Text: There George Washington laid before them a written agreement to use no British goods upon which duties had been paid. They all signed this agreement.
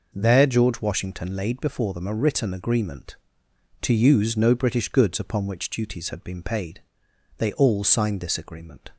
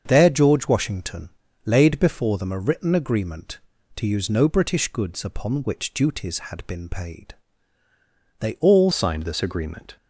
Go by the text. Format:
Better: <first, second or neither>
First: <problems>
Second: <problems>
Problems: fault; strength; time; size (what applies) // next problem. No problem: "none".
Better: first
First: none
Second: starts louder than the rest; until 1.0 s; 7 dB // pauses between "Washington" and "laid"; slight; at 1.3 s; 0.34 s long // changes voice at "signed"; from 8.9 s on; 1.0 s long